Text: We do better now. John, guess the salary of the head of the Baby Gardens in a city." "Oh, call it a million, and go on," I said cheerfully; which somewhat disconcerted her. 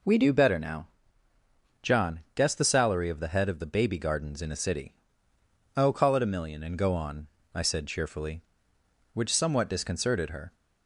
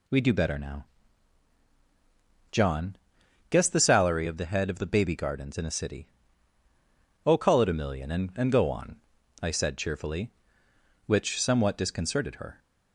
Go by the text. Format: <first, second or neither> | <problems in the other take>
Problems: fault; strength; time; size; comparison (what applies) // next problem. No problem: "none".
first | says "and" twice; at 8.3 s